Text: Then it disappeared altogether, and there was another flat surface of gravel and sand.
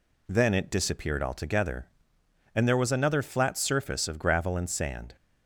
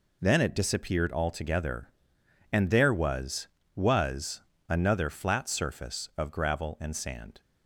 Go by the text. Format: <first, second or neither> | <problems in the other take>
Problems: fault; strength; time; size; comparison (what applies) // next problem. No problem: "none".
first | says "was" twice; at 3.7 s